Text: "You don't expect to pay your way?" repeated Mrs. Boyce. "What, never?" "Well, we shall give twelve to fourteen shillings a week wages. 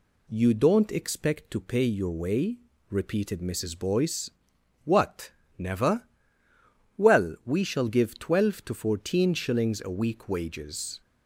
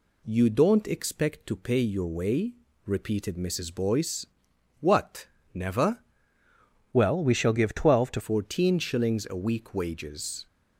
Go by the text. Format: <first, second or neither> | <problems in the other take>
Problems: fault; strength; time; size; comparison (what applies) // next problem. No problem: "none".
first | changes voice from "Well" to "to"; from 6.9 to 8.2 s; 1.3 s long